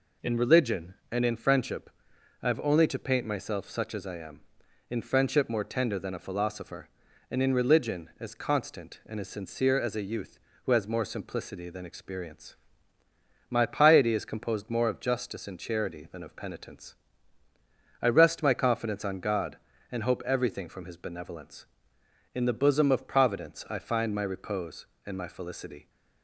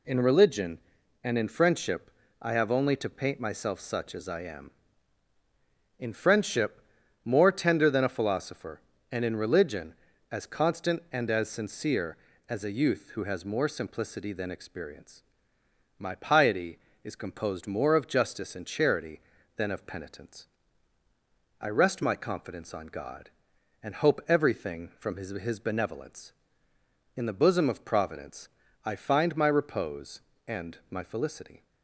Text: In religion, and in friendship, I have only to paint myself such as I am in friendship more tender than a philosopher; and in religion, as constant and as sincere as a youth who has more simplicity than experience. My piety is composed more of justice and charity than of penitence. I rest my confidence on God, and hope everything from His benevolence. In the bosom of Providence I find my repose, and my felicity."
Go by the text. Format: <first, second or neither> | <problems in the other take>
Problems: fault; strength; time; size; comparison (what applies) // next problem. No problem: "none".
first | pauses between "friendship" and "more"; at 6.8 s; 0.42 s long // says "His" twice; at 25.2 s // pauses between "Providence" and "I"; slight; at 28.4 s; 0.34 s long